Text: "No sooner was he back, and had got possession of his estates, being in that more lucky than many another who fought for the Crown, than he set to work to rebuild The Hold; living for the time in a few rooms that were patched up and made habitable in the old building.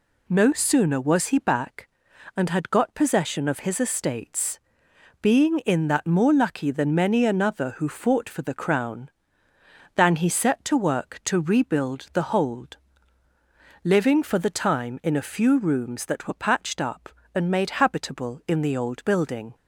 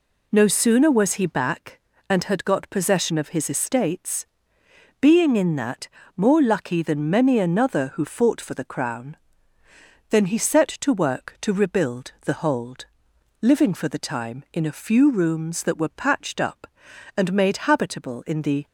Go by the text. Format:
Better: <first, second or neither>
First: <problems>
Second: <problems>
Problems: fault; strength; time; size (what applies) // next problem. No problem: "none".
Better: first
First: none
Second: pauses between "that" and "more"; slight; at 5.8 s; 0.30 s long // stops before "old building"; at 18.6 s